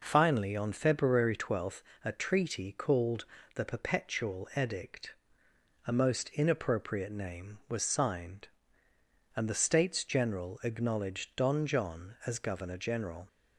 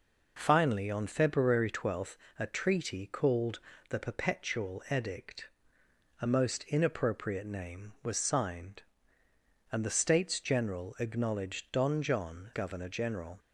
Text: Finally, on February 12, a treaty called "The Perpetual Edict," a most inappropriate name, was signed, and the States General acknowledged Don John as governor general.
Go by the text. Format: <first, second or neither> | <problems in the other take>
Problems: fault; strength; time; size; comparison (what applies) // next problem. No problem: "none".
first | pauses between "called" and "The"; slight; at 3.5 s; 0.30 s long; slight in the first // skips "as"; at 12.5 s